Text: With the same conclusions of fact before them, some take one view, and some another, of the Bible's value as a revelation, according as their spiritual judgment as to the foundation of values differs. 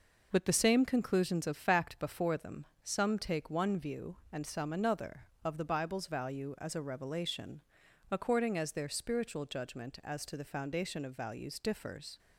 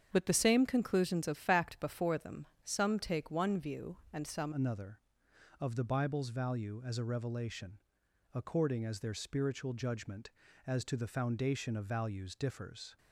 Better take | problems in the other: first | starts louder than the rest; strong; until 1.1 s; 8 dB // changes voice at "another"; from 4.5 s on; 8.4 s long

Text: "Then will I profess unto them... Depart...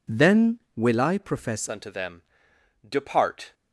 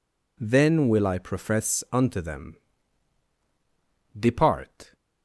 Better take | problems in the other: second | changes voice at "unto"; from 1.6 s on; 1.9 s long

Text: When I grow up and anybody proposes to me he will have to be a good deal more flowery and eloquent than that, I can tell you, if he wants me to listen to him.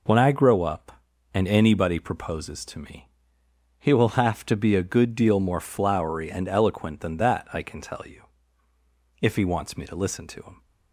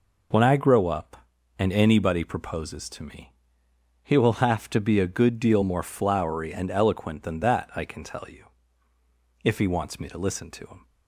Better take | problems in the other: neither | pauses between "me" and "he"; noticeable; the same in both

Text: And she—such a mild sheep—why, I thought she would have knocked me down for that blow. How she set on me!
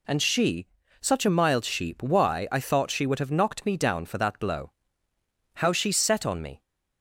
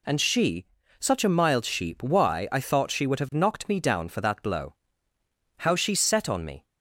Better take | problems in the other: neither | none

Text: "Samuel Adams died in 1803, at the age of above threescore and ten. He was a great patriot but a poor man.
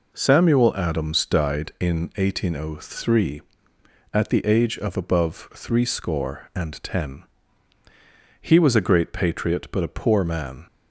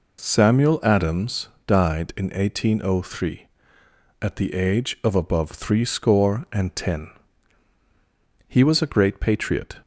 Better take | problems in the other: first | pauses between "Adams" and "died"; slight; at 1.4 s; 0.18 s long // stops before "but a poor man"; at 9.8 s

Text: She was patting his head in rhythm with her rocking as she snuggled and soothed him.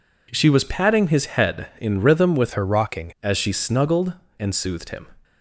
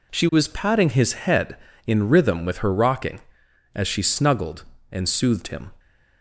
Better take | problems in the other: second | changes voice from "her" to "rocking"; from 2.5 to 3.1 s; 0.6 s long

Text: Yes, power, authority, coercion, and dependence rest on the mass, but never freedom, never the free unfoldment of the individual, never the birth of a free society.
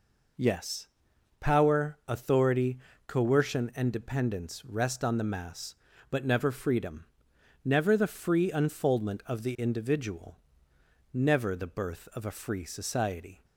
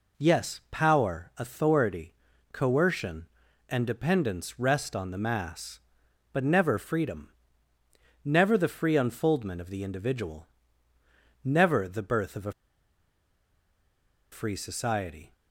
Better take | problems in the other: first | pauses between "a" and "free"; strong; at 12.5 s; 1.7 s long

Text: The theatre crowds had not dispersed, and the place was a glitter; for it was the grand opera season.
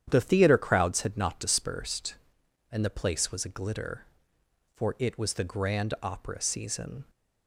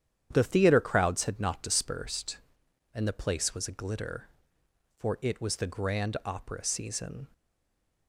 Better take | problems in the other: first | starts louder than the rest; strong; until 1.3 s; 9.5 dB; strong in the first // stays silent after the last word; slight; from 7.3 s on; 0.7 s long

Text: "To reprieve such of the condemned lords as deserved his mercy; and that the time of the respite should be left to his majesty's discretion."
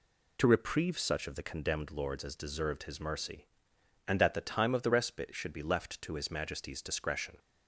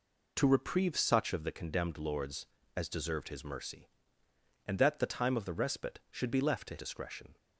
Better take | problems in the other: first | skips "his majesty's"; at 6.7 s

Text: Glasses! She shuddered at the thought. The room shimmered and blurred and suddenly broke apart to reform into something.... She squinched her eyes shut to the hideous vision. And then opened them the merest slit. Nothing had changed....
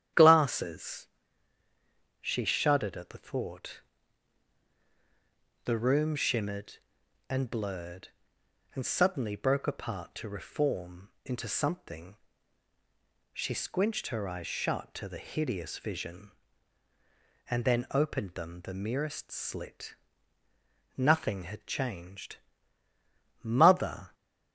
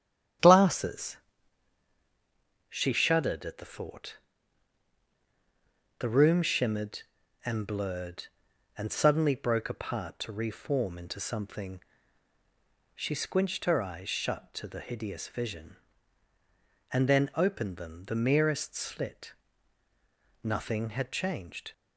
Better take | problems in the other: second | starts louder than the rest; strong; until 2.3 s; 10 dB; strong in the second // pauses between "reform" and "into"; slight; at 11.0 s; 0.16 s long // goes on to say "MOTHER"; noticeable; from 23.4 s on; 0.72 s long

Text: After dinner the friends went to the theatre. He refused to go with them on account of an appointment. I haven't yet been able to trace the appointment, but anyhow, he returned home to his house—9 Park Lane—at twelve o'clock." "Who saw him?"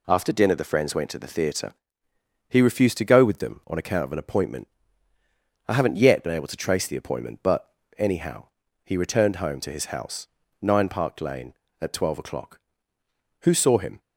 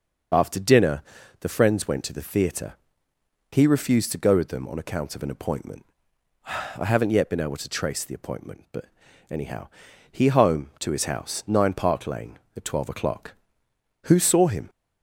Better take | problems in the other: first | starts louder than the rest; until 1.7 s; 6 dB // pauses between "dinner" and "the"; at 1.0 s; 0.38 s long // pauses between "but" and "anyhow"; at 8.8 s; 0.44 s long; slight in the first // skips "returned"; at 10.2 s

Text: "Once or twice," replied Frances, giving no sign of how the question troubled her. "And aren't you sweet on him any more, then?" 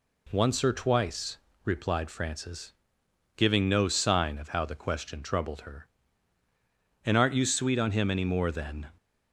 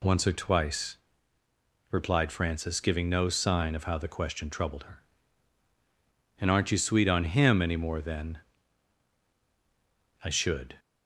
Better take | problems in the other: first | goes on to say "I should"; from 10.2 s on; 0.56 s long

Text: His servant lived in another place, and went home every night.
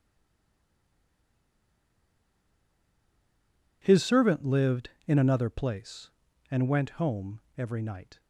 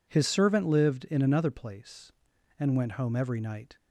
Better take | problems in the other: second | stays silent before the first word; strong; until 3.8 s; 3.8 s long // pauses between "home" and "every"; slight; at 7.4 s; 0.18 s long

